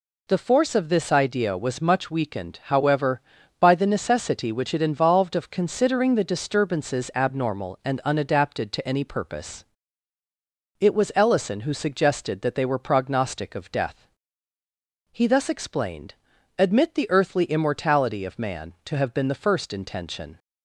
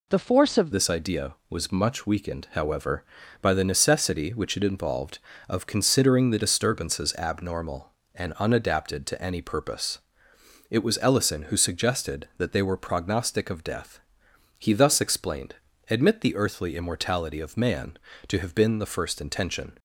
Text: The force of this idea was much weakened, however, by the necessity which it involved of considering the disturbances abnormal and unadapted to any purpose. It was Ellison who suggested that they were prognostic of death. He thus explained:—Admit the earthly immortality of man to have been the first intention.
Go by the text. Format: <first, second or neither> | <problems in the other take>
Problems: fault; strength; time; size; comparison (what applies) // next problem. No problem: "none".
first | changes voice at "this"; from 0.7 s on; 19.0 s long